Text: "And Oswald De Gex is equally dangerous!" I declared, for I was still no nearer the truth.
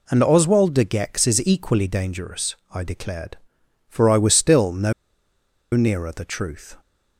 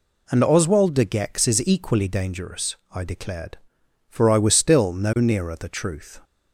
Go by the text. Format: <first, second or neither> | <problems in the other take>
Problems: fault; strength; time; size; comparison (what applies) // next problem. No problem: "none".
second | pauses between "no" and "nearer"; noticeable; at 4.9 s; 0.81 s long